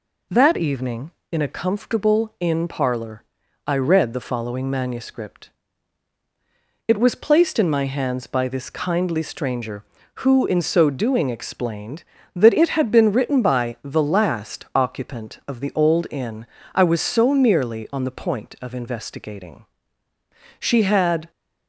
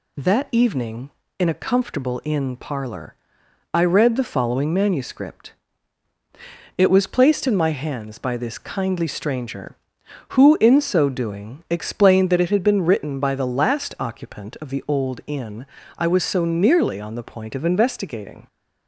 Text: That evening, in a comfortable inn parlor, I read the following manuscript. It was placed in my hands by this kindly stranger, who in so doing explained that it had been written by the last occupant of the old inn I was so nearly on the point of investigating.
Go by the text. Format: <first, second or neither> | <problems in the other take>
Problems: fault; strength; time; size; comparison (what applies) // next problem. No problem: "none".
second | pauses between "inn" and "I"; slight; at 16.4 s; 0.30 s long; slight in the second // goes on to say "She had"; noticeable; from 20.6 s on; 0.70 s long